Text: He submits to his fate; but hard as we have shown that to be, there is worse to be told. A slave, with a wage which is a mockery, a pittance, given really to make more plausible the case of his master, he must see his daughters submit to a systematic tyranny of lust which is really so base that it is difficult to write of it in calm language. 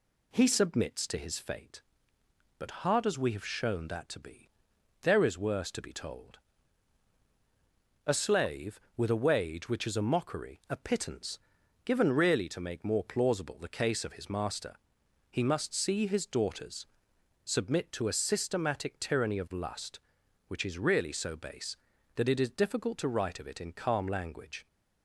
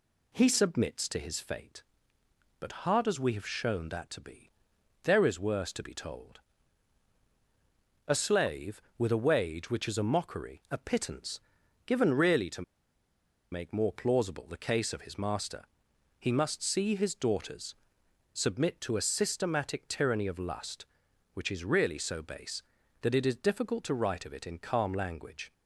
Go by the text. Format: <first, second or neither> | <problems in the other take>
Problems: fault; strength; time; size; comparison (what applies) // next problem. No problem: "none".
first | pauses between "to" and "make"; noticeable; at 12.6 s; 0.88 s long // pauses between "daughters" and "submit"; noticeable; at 17.7 s; 0.58 s long; noticeable in the first